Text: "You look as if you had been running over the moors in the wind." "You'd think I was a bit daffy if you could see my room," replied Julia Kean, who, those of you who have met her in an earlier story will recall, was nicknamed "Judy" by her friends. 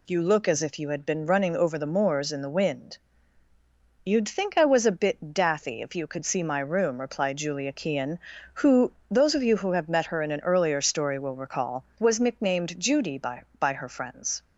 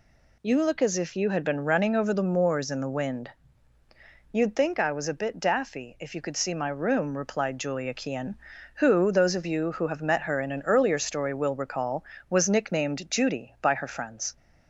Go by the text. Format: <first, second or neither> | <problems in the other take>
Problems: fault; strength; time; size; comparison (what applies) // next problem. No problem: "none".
second | says "by" twice; at 13.5 s